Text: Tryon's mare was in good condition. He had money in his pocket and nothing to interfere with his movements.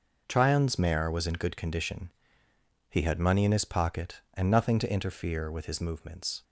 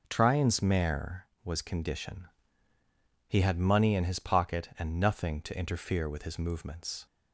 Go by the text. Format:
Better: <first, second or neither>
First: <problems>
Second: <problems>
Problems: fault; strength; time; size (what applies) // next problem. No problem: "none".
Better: first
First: none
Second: skips "in good"; at 1.5 s